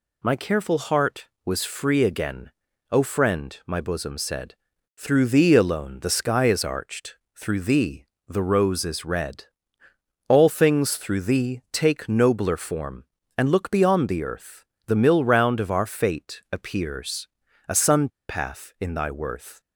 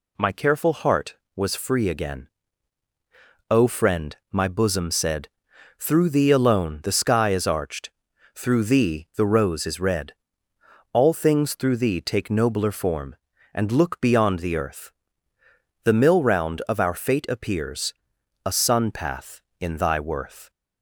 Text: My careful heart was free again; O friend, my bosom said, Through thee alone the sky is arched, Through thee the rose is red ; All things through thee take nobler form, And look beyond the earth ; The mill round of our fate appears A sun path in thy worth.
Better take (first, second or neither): second